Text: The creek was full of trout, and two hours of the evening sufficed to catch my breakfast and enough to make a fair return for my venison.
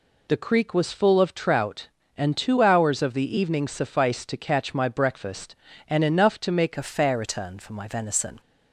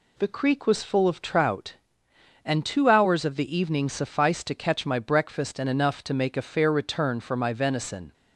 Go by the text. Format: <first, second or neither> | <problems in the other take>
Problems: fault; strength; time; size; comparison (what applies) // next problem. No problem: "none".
second | changes voice at "a"; from 6.7 s on; 1.6 s long